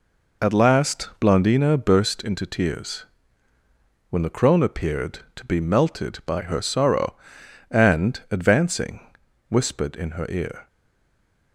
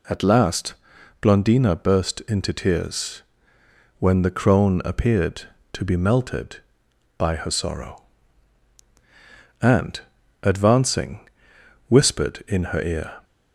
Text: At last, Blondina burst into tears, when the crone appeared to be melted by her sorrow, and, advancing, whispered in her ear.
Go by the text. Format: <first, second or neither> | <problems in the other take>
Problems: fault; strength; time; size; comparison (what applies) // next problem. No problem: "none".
second | stays silent after the last word; slight; from 10.6 s on; 0.9 s long